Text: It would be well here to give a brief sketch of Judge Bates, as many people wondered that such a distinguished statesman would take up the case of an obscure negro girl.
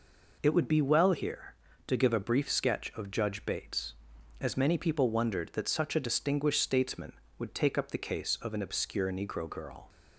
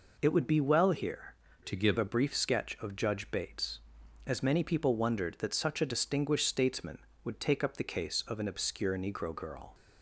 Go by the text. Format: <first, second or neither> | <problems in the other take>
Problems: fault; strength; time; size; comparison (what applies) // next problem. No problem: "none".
first | changes voice from "to" to "give"; from 1.6 to 1.9 s; 0.3 s long